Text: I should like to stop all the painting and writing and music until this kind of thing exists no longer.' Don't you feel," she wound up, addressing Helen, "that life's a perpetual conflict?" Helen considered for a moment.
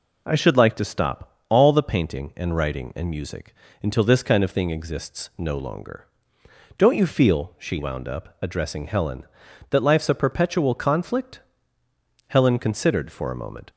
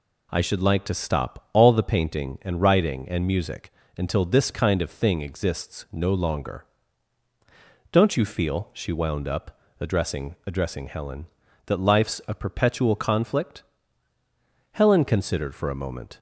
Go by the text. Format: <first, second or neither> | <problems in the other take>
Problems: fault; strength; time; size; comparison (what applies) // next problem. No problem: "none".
first | pauses between "music" and "until"; slight; at 3.7 s; 0.26 s long; slight in the first // says "addressing" twice; at 10.4 s